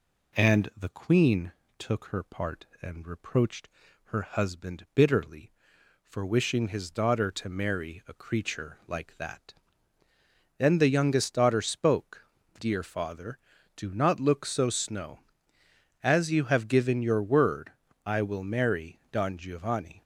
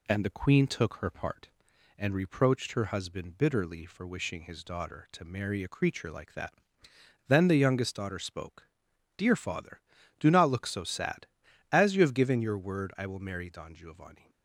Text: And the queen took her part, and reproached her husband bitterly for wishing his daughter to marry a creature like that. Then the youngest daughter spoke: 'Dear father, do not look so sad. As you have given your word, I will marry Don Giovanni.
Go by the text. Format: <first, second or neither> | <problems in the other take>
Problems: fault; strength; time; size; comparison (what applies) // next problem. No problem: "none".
second | pauses between "queen" and "took"; slight; at 1.5 s; 0.26 s long // pauses between "reproached" and "her"; slight; at 3.6 s; 0.36 s long // says "snow" for "sad"; at 14.6 s